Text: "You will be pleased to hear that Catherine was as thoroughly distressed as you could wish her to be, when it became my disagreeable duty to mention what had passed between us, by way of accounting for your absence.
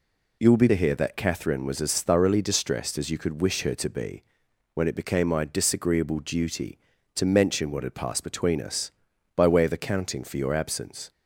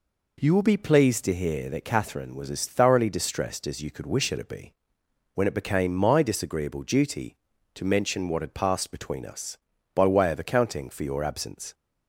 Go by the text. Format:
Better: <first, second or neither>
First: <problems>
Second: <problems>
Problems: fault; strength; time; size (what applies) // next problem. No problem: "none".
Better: second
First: skips "pleased"; at 0.6 s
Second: none